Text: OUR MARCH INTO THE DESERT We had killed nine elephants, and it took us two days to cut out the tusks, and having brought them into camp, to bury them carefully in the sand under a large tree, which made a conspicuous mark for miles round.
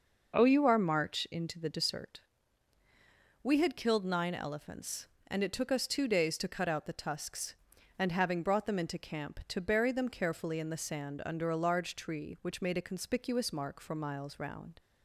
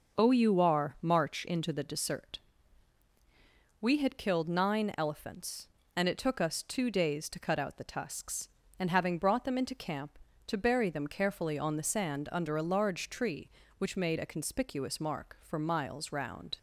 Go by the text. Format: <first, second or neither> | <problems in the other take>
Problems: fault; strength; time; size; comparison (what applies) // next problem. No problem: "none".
first | starts louder than the rest; until 1.2 s; 6 dB // pauses between "DESERT" and "We"; strong; at 2.3 s; 1.4 s long; strong in the first // says "on" for "in"; at 11.5 s